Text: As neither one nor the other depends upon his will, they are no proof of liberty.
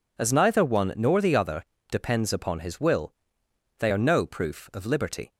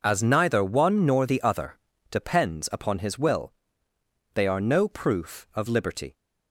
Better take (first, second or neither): neither